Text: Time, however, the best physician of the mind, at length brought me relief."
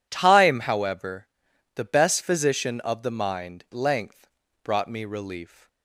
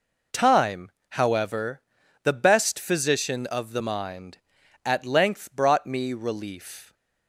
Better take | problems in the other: second | skips "at"; at 3.6 s // pauses between "length" and "brought"; slight; at 4.2 s; 0.36 s long

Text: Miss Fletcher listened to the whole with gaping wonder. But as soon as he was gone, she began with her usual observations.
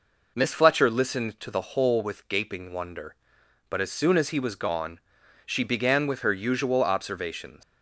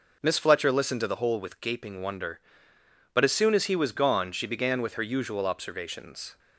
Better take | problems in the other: second | leaves "observations" unfinished; at 7.6 s; 125 ms

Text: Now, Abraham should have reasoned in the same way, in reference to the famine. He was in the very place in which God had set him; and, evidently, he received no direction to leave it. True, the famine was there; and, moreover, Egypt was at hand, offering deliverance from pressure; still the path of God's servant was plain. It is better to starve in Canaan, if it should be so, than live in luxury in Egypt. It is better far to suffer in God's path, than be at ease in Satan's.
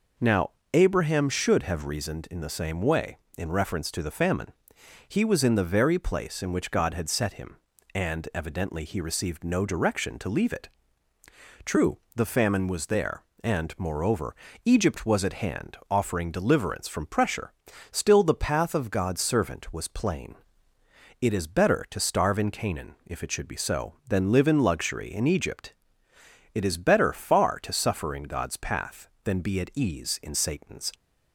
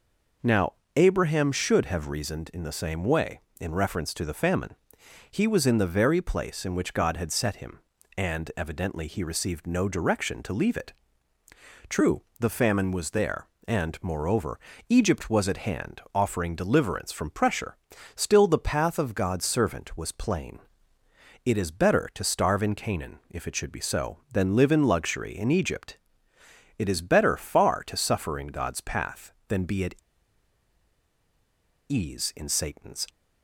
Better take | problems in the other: first | pauses between "at" and "ease"; strong; at 29.9 s; 1.9 s long

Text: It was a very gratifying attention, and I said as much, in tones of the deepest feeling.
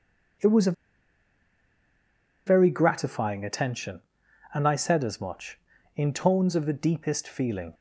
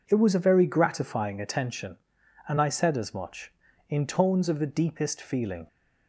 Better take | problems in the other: second | pauses between "a" and "very"; strong; at 0.7 s; 1.7 s long

